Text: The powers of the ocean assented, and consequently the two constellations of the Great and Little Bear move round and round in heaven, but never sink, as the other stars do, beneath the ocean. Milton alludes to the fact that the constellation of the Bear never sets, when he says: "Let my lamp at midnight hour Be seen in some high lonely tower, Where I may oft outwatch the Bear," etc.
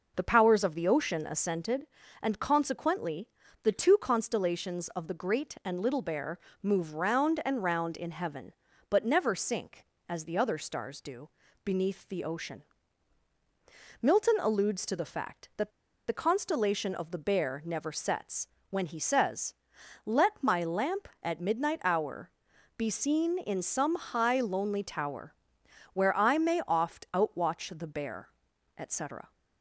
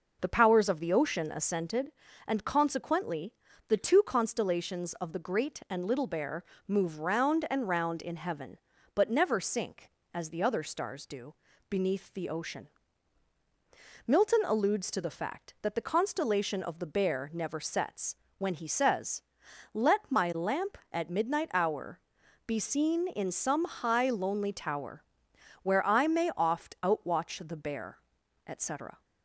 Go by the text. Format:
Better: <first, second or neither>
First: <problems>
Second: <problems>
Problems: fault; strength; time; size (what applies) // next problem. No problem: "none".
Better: second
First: pauses between "consequently" and "the"; slight; at 3.2 s; 0.36 s long // pauses between "Bear" and "move"; slight; at 6.3 s; 0.24 s long // pauses between "that" and "the"; at 15.7 s; 0.37 s long // pauses between "hour" and "Be"; noticeable; at 22.2 s; 0.48 s long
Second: pauses between "consequently" and "the"; slight; at 3.3 s; 0.36 s long // pauses between "Bear" and "move"; slight; at 6.4 s; 0.24 s long // pauses between "hour" and "Be"; noticeable; at 21.9 s; 0.48 s long